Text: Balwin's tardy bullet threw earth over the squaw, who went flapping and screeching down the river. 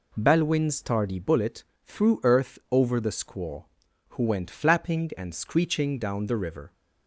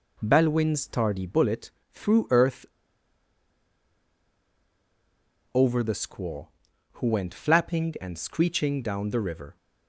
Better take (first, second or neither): first